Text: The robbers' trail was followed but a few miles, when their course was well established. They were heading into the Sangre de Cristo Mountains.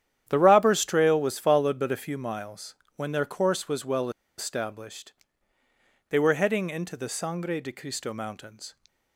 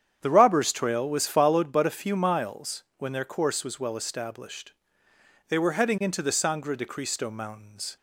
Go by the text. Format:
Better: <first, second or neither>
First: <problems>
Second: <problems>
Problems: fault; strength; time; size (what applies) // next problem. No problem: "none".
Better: second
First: starts louder than the rest; strong; until 1.3 s; 10.5 dB // pauses between "well" and "established"; slight; at 4.0 s; 0.28 s long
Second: starts louder than the rest; strong; until 1.2 s; 8.5 dB